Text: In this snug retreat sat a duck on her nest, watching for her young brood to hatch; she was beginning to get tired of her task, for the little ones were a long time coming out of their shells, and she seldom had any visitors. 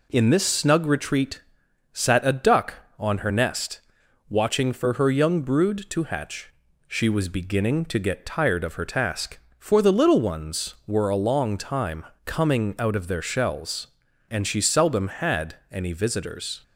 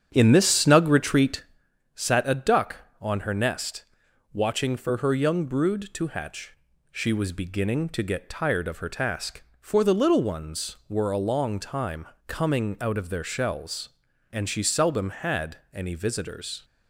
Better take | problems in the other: first | starts louder than the rest; strong; until 1.7 s; 9 dB // pauses between "retreat" and "sat"; noticeable; at 1.4 s; 0.50 s long; noticeable in the first // pauses between "time" and "coming"; slight; at 12.0 s; 0.20 s long; slight in the first // pauses between "had" and "any"; slight; at 15.5 s; 0.16 s long; slight in the first

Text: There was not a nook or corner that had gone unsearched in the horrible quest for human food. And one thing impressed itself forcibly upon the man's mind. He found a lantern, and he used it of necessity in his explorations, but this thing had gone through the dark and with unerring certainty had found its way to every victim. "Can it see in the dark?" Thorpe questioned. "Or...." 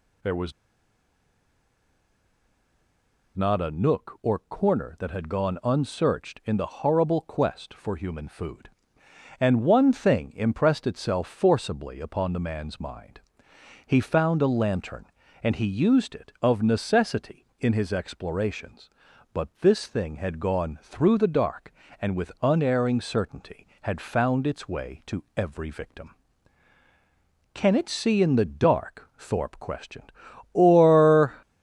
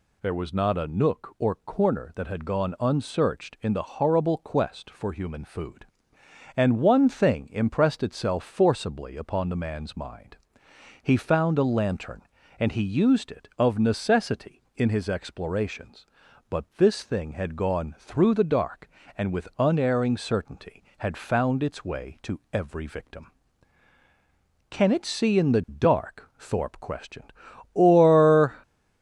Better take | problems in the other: second | pauses between "was" and "not"; strong; at 0.5 s; 2.8 s long

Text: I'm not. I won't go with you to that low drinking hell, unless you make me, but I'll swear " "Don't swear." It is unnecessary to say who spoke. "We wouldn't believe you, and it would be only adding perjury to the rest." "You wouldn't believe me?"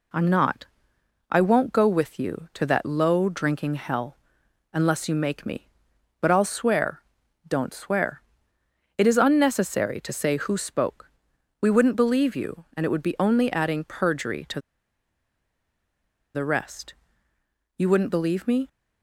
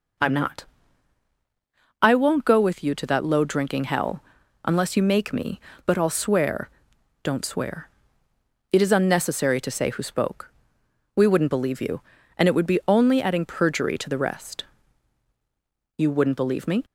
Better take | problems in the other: second | pauses between "to" and "the"; strong; at 14.6 s; 1.7 s long

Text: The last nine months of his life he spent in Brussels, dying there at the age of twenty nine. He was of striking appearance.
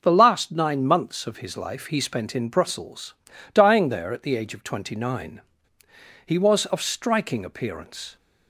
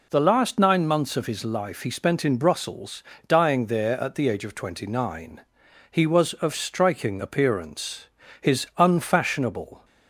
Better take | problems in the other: first | goes on to say "His unfashionable"; from 8.4 s on; 1.4 s long

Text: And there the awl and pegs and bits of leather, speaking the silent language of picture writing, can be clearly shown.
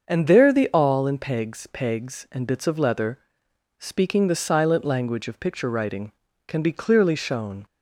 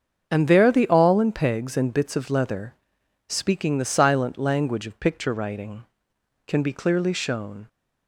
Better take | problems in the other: second | starts louder than the rest; until 1.0 s; 6.5 dB; also in the second // says "pegs" twice; at 1.6 s

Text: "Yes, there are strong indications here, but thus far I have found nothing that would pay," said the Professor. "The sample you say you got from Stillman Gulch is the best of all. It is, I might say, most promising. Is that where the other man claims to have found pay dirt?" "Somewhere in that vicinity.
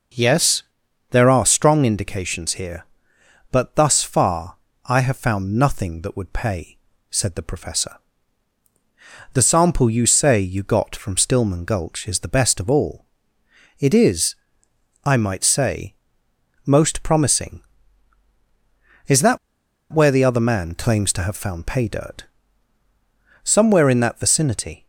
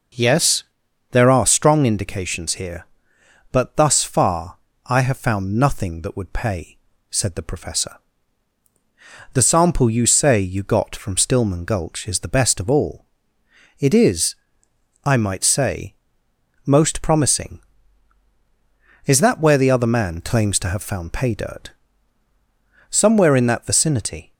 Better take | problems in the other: second | pauses between "far" and "I"; slight; at 4.5 s; 0.28 s long; slight in the second // pauses between "that" and "where"; noticeable; at 19.3 s; 0.54 s long

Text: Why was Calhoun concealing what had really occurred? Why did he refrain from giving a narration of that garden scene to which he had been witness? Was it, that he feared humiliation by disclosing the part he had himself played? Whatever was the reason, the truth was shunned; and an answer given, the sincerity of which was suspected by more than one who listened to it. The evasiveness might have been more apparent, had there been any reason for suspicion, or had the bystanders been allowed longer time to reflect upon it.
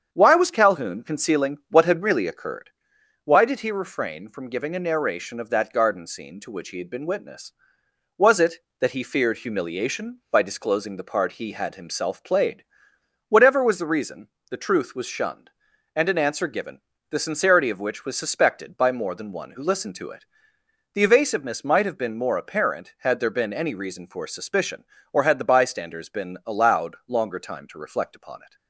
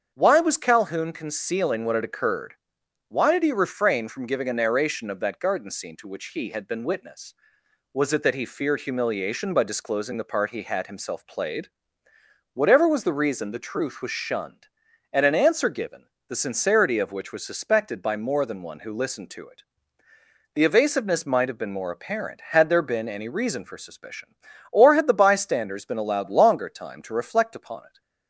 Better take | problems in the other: first | starts louder than the rest; strong; until 1.1 s; 7.5 dB; strong in the first // skips "really"; at 2.0 s

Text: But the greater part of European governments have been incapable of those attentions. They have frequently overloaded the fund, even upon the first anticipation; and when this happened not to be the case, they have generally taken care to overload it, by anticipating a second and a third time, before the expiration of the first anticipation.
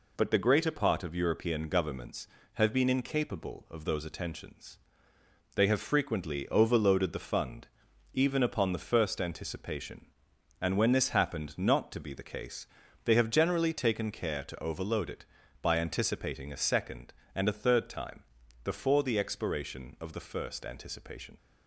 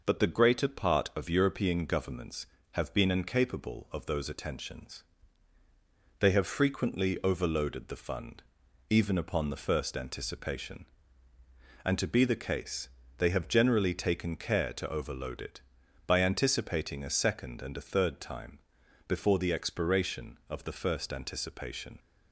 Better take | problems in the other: first | skips "when this happened not"; at 11.9 s

